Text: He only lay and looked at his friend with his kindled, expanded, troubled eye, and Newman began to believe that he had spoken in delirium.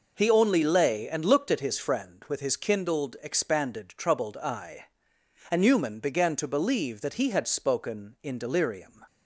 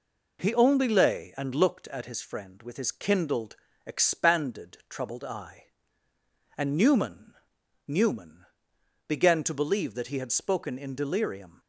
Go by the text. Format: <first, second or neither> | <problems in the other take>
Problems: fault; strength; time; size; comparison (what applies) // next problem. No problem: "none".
first | says "Newman" twice; at 7.8 s